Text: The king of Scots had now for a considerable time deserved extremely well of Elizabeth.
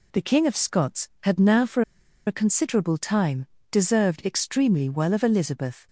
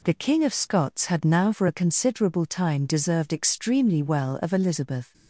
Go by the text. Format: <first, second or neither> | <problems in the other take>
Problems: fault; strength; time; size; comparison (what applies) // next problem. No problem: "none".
second | pauses between "for" and "a"; at 1.8 s; 0.44 s long // pauses between "time" and "deserved"; slight; at 3.4 s; 0.26 s long